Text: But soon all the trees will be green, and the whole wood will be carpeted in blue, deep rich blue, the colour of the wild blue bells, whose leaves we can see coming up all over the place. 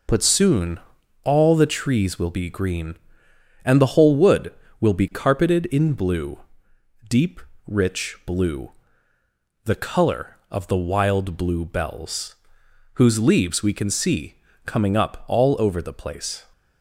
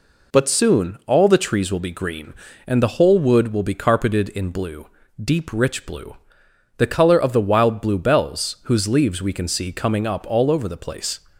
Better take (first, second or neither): second